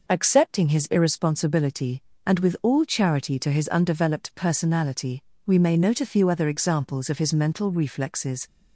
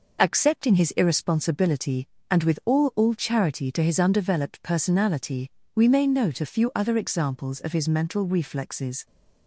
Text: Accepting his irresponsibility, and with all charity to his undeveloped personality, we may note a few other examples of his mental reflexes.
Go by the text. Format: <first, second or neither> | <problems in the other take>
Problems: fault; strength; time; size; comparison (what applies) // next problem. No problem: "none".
first | says "all" twice; at 2.9 s